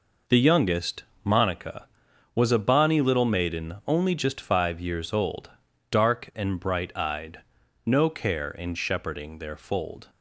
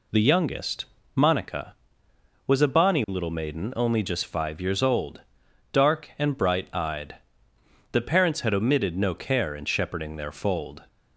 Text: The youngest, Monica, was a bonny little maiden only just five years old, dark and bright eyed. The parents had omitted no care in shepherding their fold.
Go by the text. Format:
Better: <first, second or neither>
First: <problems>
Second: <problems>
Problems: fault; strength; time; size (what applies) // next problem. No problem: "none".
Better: second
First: skips "The parents had omitted"; at 7.6 s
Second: none